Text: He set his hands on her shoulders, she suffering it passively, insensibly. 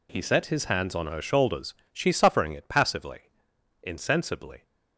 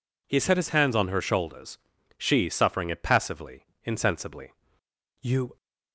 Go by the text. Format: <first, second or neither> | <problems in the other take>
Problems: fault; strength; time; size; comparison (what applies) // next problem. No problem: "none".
first | goes on to say "You"; slight; from 5.2 s on; 0.36 s long